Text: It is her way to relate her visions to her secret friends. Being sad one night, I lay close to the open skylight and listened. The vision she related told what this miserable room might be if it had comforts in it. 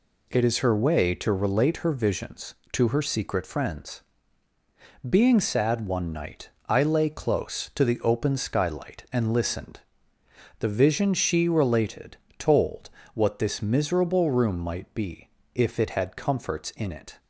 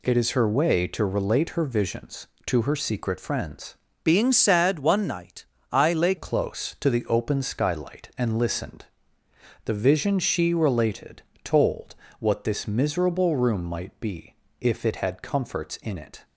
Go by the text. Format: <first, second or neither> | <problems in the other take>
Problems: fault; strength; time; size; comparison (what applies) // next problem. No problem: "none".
first | changes voice from "Being" to "lay"; from 4.0 to 6.1 s; 2.1 s long // pauses between "related" and "told"; slight; at 11.2 s; 0.22 s long; slight in the first // pauses between "told" and "what"; slight; at 11.9 s; 0.26 s long; slight in the first // pauses between "be" and "if"; slight; at 14.3 s; 0.26 s long; slight in the first